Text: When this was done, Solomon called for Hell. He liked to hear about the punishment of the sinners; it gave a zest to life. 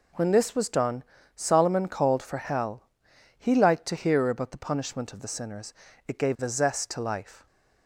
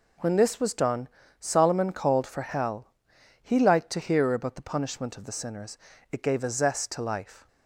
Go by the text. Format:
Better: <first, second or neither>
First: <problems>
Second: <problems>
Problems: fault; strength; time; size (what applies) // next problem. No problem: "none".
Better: neither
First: none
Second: none